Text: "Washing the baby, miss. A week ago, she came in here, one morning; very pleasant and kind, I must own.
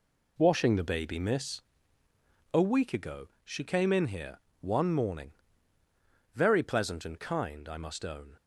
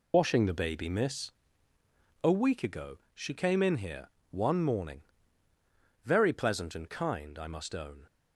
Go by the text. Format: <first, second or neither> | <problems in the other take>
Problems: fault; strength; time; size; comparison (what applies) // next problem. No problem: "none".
first | loses the start of "Washing"; at 0.1 s; 60 ms